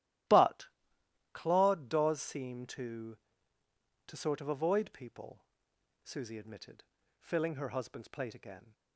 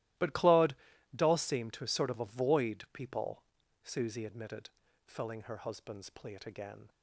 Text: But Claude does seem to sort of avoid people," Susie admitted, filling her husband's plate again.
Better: second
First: starts louder than the rest; strong; until 1.9 s; 15 dB // pauses between "But" and "Claude"; noticeable; at 0.6 s; 0.66 s long // says "to" twice; at 4.0 s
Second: starts louder than the rest; strong; until 1.5 s; 16.5 dB

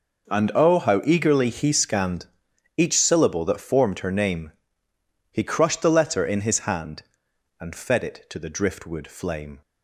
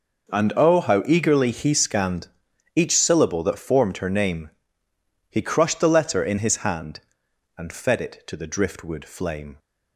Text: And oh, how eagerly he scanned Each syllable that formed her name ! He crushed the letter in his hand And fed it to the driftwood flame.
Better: neither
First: pauses between "scanned" and "Each"; noticeable; at 2.2 s; 0.49 s long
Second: pauses between "scanned" and "Each"; noticeable; at 2.2 s; 0.46 s long

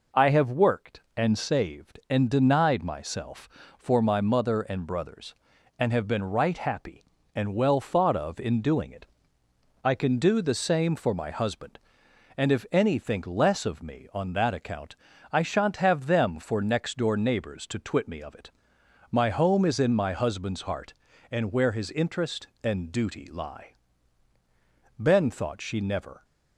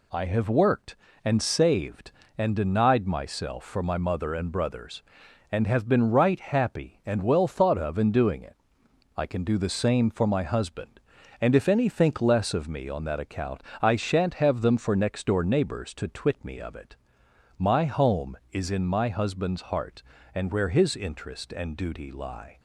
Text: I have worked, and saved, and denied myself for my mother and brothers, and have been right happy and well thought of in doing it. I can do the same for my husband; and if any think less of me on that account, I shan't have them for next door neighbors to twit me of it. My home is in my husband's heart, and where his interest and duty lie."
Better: second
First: goes on to say "Ben thought she never"; noticeable; from 24.9 s on; 1.2 s long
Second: none

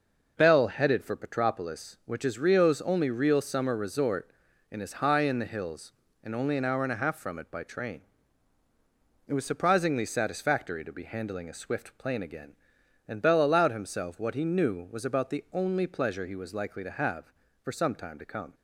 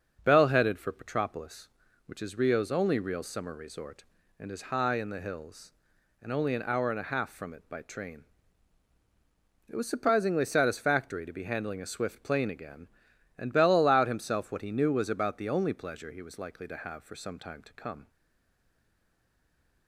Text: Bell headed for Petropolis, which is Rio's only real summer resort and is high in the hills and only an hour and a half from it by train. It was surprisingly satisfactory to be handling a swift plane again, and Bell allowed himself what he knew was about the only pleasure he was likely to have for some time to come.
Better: first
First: none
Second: starts louder than the rest; until 1.2 s; 6 dB // stays silent after the last word; noticeable; from 18.0 s on; 1.8 s long

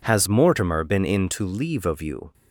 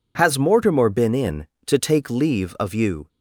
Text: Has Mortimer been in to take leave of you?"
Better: second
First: skips "take"; at 1.4 s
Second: none

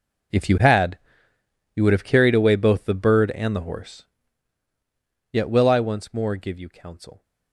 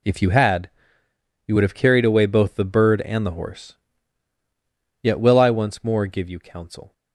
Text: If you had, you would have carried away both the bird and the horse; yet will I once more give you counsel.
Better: second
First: gets quieter; strong; throughout; 19 dB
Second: none

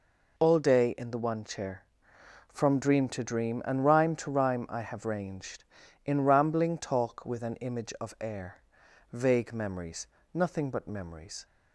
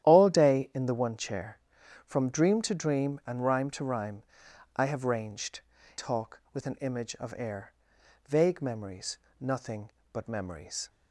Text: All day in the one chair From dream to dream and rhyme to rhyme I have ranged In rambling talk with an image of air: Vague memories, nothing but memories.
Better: first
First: none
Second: starts louder than the rest; strong; until 1.1 s; 11.5 dB // pauses between "rhyme" and "I"; noticeable; at 4.2 s; 0.50 s long // skips "In rambling"; at 5.7 s

